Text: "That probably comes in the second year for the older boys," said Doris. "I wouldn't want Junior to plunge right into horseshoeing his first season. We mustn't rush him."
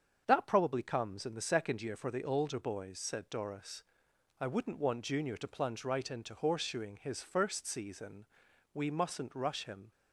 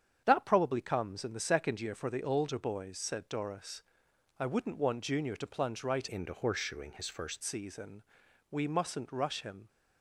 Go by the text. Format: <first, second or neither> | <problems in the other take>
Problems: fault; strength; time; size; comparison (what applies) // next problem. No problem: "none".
first | starts louder than the rest; strong; until 1.2 s; 8 dB; strong in the first // changes voice from "into" to "first"; from 6.0 to 7.4 s; 1.4 s long